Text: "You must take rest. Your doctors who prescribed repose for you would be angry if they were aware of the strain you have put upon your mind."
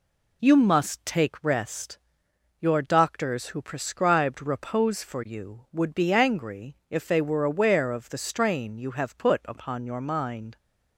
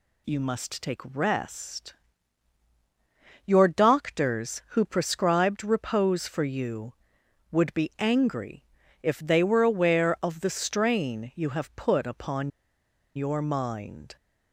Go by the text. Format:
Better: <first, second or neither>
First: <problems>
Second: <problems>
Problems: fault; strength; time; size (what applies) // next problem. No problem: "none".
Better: first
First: none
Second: pauses between "angry" and "if"; at 8.6 s; 0.38 s long // pauses between "upon" and "your"; noticeable; at 12.5 s; 0.65 s long